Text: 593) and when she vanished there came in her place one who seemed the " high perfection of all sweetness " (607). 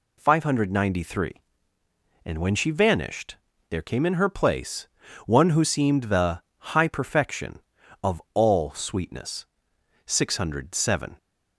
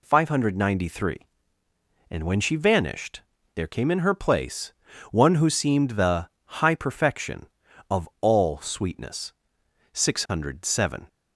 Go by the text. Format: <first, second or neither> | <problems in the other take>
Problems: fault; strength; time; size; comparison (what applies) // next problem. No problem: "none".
neither | pauses between "vanished" and "there"; slight; the same in both // pauses between "place" and "one"; the same in both